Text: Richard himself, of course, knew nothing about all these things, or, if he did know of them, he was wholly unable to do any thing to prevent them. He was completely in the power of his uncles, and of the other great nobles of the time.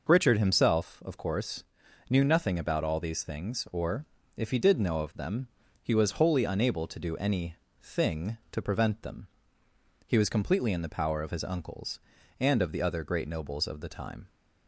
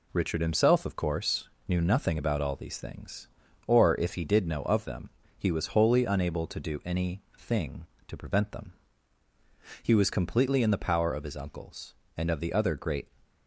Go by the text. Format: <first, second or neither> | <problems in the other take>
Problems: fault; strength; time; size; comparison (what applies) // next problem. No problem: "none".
first | pauses between "any" and "thing"; slight; at 7.2 s; 0.16 s long; slight in the first // stops before "nobles of the time"; at 13.2 s